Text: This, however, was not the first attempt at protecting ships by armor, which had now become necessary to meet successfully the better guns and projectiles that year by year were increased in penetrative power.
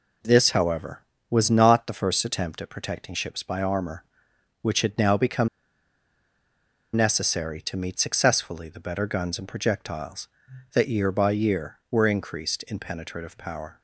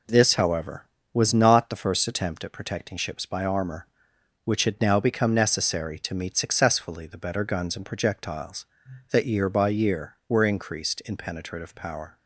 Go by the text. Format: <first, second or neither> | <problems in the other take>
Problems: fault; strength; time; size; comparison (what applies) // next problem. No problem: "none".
second | pauses between "become" and "necessary"; strong; at 5.4 s; 1.4 s long